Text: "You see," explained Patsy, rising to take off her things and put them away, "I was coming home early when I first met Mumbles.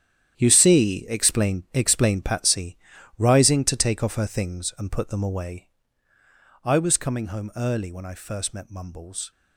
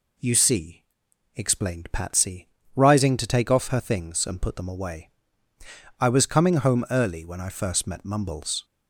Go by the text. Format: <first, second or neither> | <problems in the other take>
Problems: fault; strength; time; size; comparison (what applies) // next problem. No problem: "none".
second | starts louder than the rest; strong; until 1.3 s; 10 dB // says "explained" twice; at 1.7 s